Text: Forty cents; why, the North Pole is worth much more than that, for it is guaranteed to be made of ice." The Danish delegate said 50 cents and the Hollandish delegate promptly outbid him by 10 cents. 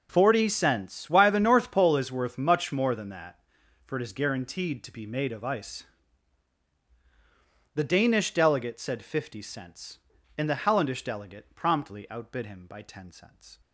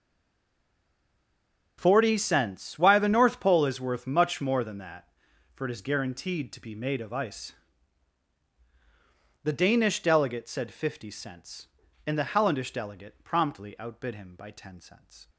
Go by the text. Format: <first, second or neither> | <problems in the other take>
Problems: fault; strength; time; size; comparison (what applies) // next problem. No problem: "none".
first | stays silent before the first word; noticeable; until 1.7 s; 1.7 s long